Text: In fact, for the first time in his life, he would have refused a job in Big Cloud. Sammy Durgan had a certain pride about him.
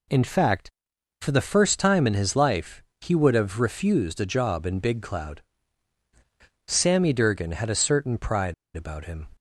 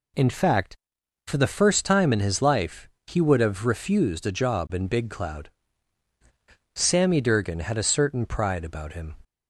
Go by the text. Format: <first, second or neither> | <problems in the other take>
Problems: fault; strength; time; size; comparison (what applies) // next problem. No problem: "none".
second | pauses between "pride" and "about"; slight; at 8.5 s; 0.21 s long